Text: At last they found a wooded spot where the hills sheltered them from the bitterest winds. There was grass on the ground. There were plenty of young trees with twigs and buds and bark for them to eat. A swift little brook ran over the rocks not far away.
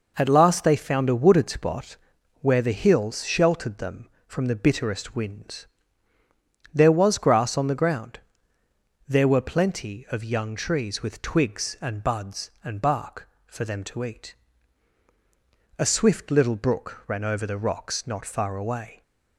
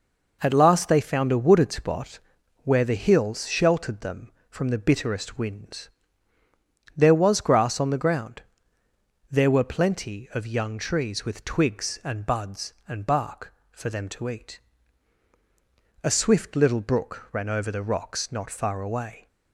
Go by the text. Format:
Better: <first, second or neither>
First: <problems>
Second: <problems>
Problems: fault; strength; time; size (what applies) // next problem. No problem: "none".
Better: neither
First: pauses between "spot" and "where"; at 1.9 s; 0.44 s long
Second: pauses between "spot" and "where"; at 2.1 s; 0.44 s long